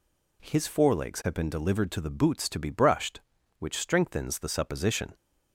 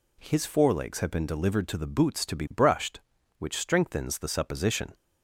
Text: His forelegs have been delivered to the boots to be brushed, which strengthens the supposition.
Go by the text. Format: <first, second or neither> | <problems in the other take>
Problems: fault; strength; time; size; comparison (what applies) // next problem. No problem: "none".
neither | none